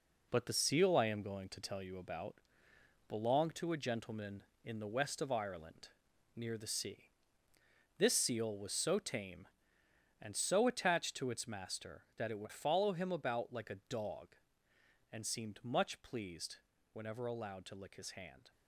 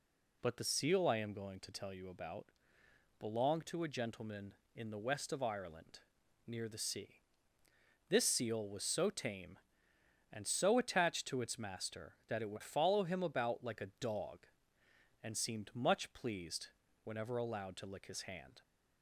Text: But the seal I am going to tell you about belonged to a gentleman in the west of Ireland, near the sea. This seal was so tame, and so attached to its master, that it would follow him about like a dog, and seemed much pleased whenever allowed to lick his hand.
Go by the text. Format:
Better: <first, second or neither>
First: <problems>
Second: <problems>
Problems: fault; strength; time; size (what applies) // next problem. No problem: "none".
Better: second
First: gets quieter; throughout; 7 dB // pauses between "about" and "belonged"; noticeable; at 2.3 s; 0.74 s long // pauses between "pleased" and "whenever"; slight; at 16.5 s; 0.36 s long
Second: pauses between "about" and "belonged"; noticeable; at 2.4 s; 0.74 s long // pauses between "pleased" and "whenever"; slight; at 16.6 s; 0.36 s long